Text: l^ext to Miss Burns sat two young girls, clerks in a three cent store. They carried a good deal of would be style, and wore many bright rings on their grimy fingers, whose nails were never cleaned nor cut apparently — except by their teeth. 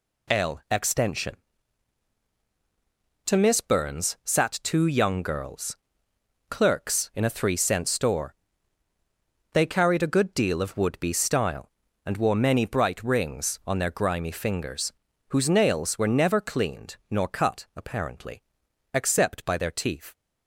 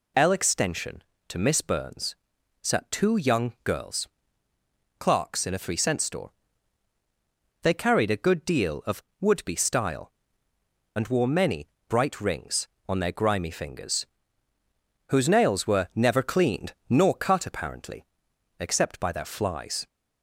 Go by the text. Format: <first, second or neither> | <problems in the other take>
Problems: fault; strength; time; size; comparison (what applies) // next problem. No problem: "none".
first | pauses between "Burns" and "sat"; noticeable; at 2.1 s; 0.48 s long // pauses between "many" and "bright"; slight; at 11.6 s; 0.22 s long // says "flies" for "teeth"; at 19.2 s